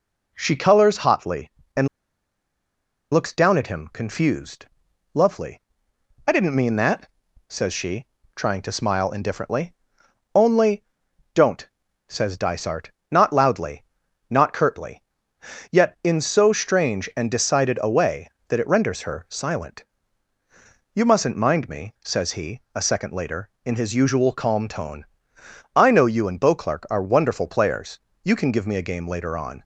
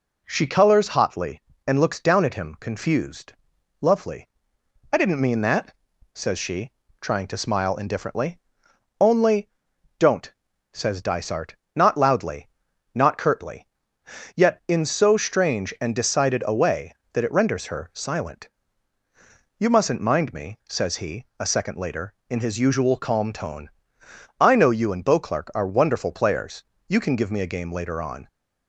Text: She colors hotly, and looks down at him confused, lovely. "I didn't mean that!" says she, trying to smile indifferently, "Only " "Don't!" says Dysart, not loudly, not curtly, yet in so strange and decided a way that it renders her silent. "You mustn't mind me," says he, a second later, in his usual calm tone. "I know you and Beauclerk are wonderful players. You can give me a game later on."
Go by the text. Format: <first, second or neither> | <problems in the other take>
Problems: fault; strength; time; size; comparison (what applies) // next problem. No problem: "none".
second | pauses between "and" and "looks"; strong; at 1.8 s; 1.2 s long